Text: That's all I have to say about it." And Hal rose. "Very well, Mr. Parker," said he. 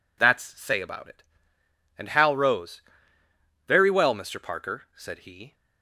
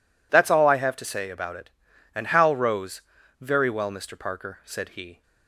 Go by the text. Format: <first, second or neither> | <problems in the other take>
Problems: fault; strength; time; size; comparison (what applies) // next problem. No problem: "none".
second | skips "all I have to"; at 0.4 s